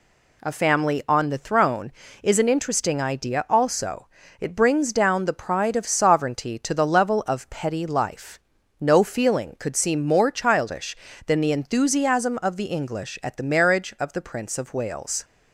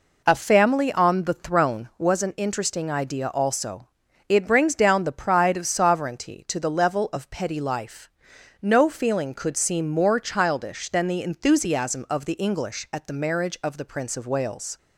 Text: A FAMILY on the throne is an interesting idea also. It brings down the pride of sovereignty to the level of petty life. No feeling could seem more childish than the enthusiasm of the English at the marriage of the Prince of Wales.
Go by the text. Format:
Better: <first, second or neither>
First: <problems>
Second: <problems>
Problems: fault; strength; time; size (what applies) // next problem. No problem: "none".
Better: first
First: none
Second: says "was" for "is"; at 1.9 s